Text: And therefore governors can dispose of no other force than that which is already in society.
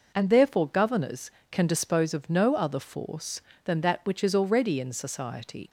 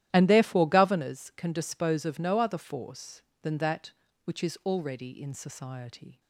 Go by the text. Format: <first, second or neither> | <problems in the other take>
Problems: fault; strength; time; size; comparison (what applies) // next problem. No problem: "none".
first | starts louder than the rest; strong; until 1.1 s; 13 dB